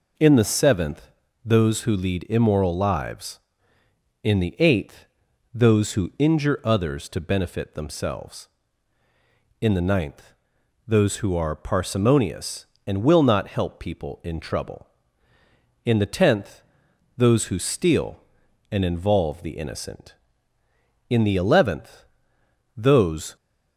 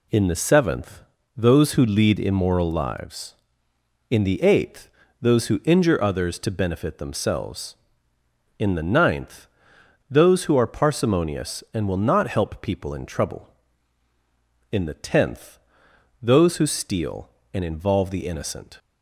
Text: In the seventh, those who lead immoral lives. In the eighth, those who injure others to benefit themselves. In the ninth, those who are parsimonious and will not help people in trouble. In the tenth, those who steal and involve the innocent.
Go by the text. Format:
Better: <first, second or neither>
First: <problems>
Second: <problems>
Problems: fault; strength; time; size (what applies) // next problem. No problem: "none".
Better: second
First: goes on to say "In the eleventh those"; strong; from 21.0 s on; 2.2 s long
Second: none